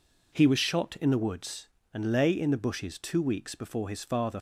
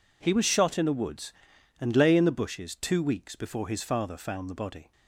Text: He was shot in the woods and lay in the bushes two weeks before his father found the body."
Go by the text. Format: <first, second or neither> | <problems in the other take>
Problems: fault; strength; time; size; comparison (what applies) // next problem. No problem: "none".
second | stops before "found the body"; at 4.3 s